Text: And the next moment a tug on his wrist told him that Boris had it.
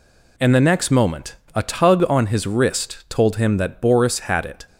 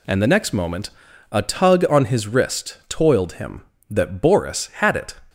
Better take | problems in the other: first | pauses between "moment" and "a"; at 0.9 s; 0.42 s long; slight in the first // says "toiled" for "told"; at 2.8 s

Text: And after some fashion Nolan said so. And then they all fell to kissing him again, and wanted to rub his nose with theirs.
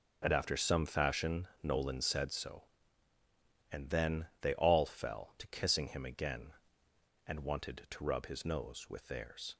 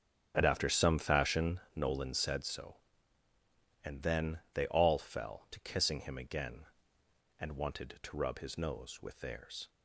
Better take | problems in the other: first | starts louder than the rest; until 1.7 s; 7 dB

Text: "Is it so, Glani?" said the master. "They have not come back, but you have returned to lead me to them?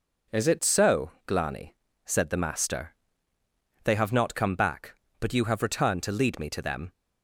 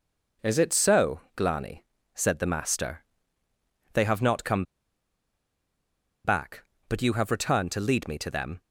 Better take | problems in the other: first | pauses between "come" and "back"; strong; at 4.6 s; 1.6 s long

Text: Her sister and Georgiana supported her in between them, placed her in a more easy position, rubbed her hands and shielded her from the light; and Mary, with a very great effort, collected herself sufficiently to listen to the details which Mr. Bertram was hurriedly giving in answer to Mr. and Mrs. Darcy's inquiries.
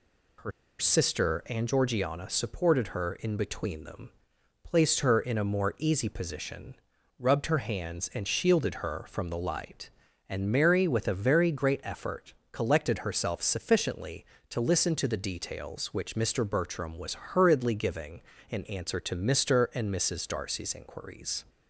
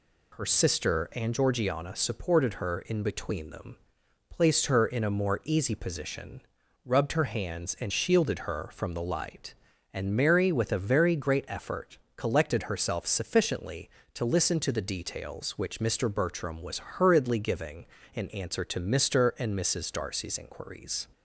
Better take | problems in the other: second | pauses between "Her" and "sister"; slight; at 0.5 s; 0.29 s long

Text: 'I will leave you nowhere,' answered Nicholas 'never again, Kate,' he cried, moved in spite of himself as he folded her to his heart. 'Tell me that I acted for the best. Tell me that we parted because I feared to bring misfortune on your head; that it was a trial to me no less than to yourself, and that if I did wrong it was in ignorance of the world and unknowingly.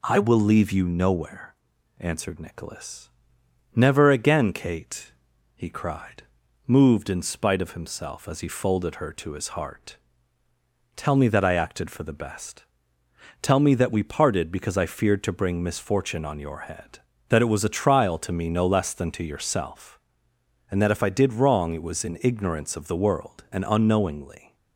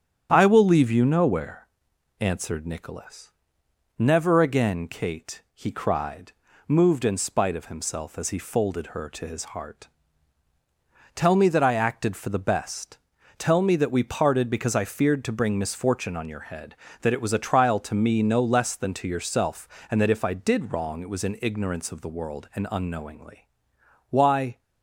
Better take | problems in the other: first | starts louder than the rest; strong; until 1.3 s; 9 dB // pauses between "Nicholas" and "never"; noticeable; at 3.3 s; 0.66 s long; noticeable in the first // goes on to say "Why"; slight; from 24.1 s on; 0.48 s long

